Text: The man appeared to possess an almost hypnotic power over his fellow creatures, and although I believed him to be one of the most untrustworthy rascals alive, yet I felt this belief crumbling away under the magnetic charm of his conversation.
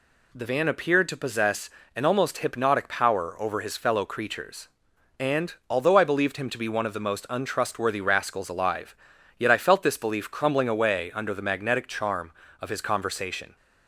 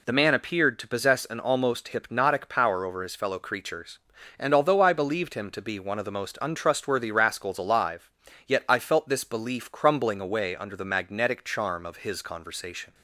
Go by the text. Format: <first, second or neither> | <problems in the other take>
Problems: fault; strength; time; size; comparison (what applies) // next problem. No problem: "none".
second | says "van" for "man"; at 0.4 s // pauses between "possess" and "an"; slight; at 1.6 s; 0.24 s long // pauses between "and" and "although"; slight; at 5.5 s; 0.16 s long